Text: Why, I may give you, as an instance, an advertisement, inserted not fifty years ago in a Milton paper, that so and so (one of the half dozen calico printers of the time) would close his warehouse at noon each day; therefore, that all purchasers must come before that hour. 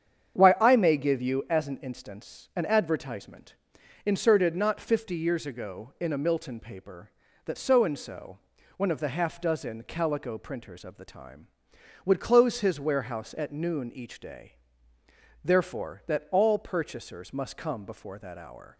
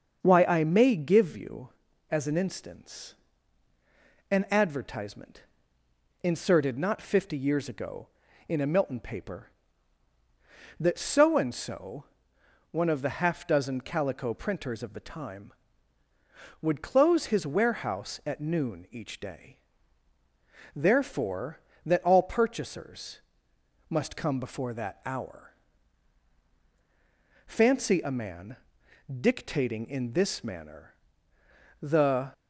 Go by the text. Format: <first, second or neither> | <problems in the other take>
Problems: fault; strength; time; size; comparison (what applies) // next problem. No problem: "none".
first | starts louder than the rest; until 1.2 s; 6.5 dB; strong in the first // pauses between "purchasers" and "must"; noticeable; at 23.1 s; 0.70 s long // goes on to say "Fancy a man dictating in this manner the"; strong; from 27.4 s on; 4.8 s long